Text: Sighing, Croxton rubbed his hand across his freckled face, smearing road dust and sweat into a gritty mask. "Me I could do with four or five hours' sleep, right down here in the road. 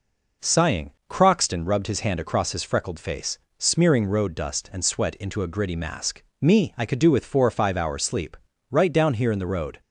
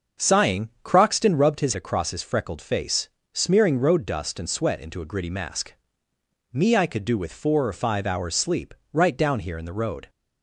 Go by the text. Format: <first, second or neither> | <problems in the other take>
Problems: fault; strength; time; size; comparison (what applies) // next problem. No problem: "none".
first | starts louder than the rest; until 1.3 s; 6.5 dB // skips "hand"; at 1.7 s